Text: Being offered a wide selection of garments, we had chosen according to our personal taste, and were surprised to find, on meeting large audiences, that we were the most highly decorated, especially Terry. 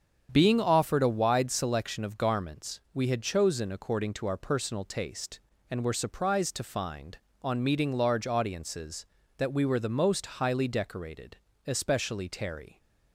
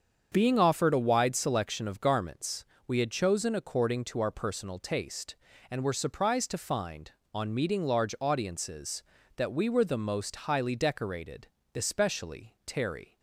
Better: neither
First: starts louder than the rest; strong; until 1.3 s; 8 dB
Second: starts louder than the rest; strong; until 1.3 s; 7 dB

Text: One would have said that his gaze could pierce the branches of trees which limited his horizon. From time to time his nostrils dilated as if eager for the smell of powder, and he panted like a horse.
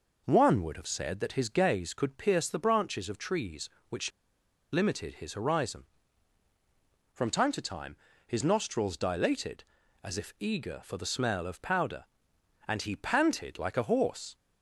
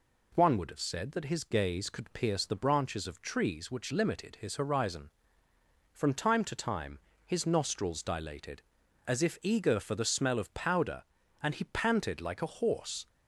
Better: second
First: pauses between "which" and "limited"; noticeable; at 4.1 s; 0.62 s long // pauses between "time" and "his"; slight; at 7.9 s; 0.30 s long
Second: pauses between "time" and "his"; slight; at 6.9 s; 0.26 s long

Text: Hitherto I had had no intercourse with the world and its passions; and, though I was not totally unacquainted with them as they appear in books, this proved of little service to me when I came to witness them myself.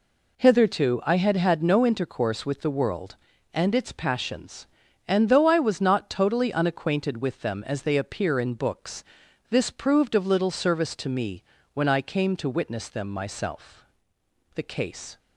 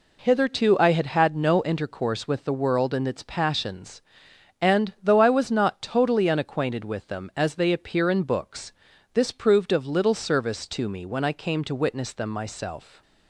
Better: second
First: pauses between "me" and "when"; slight; at 11.4 s; 0.32 s long // goes on to say "The case"; noticeable; from 14.5 s on; 0.64 s long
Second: none

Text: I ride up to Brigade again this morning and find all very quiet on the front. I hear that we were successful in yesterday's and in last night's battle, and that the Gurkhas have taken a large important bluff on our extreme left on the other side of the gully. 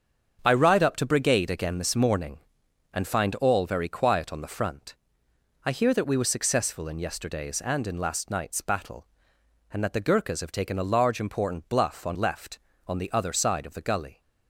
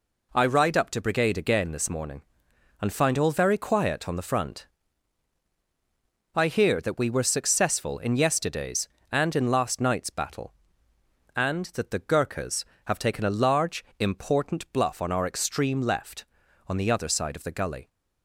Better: second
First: starts louder than the rest; until 1.4 s; 7 dB // skips "our extreme"; at 12.1 s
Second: none

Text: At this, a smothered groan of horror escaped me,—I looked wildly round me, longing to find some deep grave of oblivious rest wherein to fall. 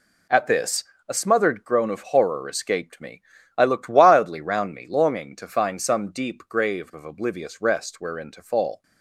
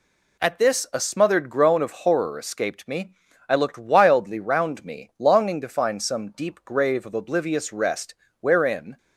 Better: first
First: none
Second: pauses between "rest" and "wherein"; slight; at 8.1 s; 0.26 s long // stops before "to fall"; at 8.9 s

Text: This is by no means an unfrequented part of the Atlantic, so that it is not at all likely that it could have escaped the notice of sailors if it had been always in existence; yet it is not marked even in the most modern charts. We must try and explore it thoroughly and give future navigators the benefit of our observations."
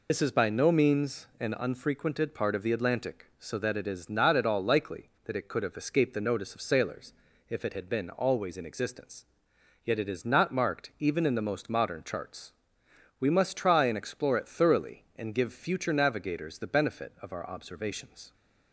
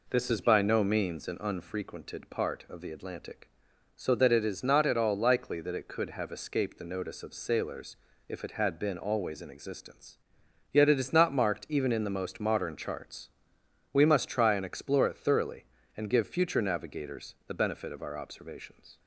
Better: second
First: loses the start of "This"; at 0.0 s; 90 ms // pauses between "sailors" and "if"; at 7.1 s; 0.38 s long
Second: pauses between "sailors" and "if"; slight; at 7.9 s; 0.28 s long

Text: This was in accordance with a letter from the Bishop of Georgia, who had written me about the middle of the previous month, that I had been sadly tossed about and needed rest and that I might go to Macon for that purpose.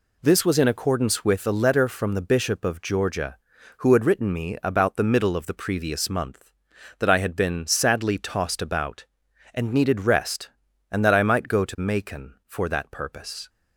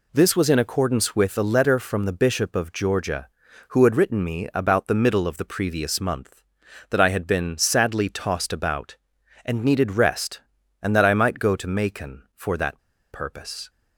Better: first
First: none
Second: pauses between "that" and "purpose"; slight; at 12.7 s; 0.32 s long

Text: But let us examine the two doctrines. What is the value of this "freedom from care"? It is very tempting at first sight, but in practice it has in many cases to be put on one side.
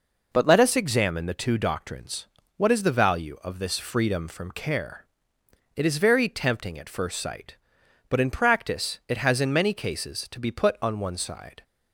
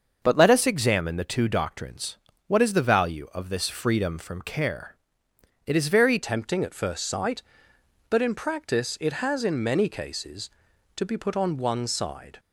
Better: first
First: none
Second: starts louder than the rest; until 1.2 s; 6.5 dB // changes voice at "tempting"; from 6.2 s on; 6.1 s long

